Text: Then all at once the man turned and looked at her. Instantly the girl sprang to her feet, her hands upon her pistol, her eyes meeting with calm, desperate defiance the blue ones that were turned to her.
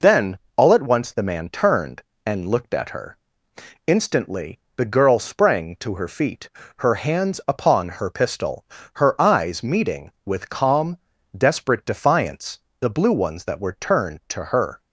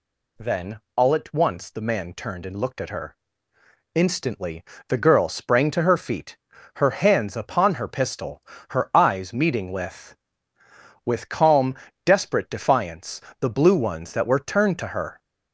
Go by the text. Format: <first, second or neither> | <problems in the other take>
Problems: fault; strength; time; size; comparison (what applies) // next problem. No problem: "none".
first | pauses between "Then" and "all"; slight; at 0.8 s; 0.16 s long; slight in the first // pauses between "Instantly" and "the"; slight; at 4.6 s; 0.26 s long; slight in the first // says "with" twice; at 11.0 s // pauses between "defiance" and "the"; slight; at 13.2 s; 0.18 s long; slight in the first